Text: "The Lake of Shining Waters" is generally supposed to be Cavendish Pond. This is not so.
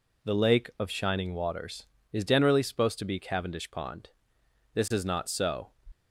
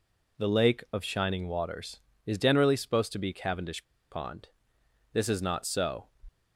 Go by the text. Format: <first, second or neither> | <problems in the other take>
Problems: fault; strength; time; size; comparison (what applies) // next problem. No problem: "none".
first | pauses between "Cavendish" and "Pond"; slight; at 3.8 s; 0.26 s long